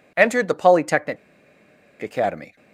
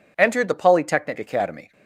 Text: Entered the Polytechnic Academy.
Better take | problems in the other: second | pauses between "Polytechnic" and "Academy"; noticeable; at 1.1 s; 0.84 s long

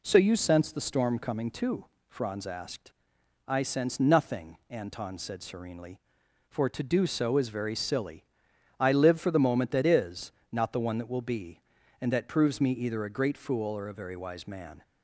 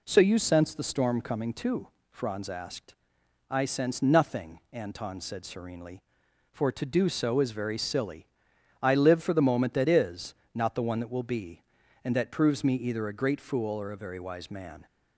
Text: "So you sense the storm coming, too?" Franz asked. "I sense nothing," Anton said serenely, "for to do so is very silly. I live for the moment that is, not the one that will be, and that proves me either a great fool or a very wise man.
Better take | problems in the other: neither | none

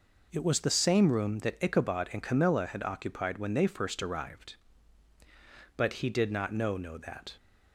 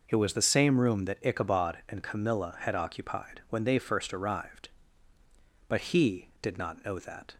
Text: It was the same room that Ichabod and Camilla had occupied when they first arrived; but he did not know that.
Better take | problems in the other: second | says "know" twice; at 6.7 s

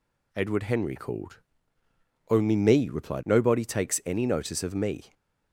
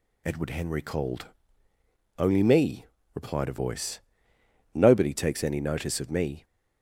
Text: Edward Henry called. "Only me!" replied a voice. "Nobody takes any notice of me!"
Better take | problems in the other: second | skips "a voice"; at 3.2 s

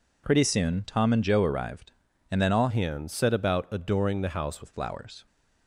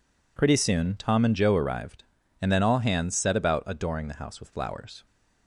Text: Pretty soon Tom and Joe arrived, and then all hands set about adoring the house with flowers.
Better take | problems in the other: second | changes voice from "hands" to "house"; from 2.6 to 4.6 s; 2.0 s long

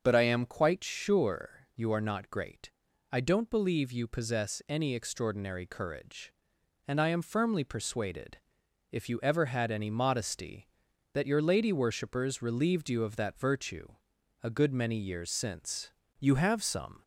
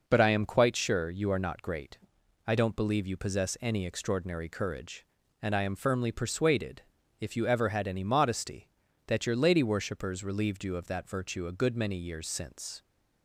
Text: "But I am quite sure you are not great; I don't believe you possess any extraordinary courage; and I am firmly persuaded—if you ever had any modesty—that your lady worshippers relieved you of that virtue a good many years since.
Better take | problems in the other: second | starts louder than the rest; until 1.0 s; 6.5 dB // pauses between "virtue" and "a"; noticeable; at 13.9 s; 0.50 s long // goes on to say "You have some"; noticeable; from 16.1 s on; 0.84 s long

